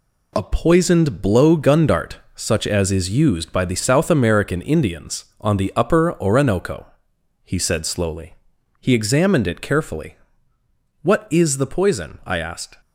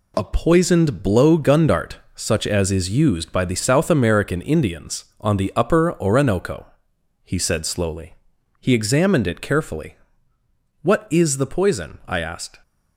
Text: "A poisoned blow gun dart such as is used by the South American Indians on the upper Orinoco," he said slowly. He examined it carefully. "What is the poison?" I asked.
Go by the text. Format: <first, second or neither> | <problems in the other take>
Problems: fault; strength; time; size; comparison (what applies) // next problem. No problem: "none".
neither | pauses between "dart" and "such"; slight; the same in both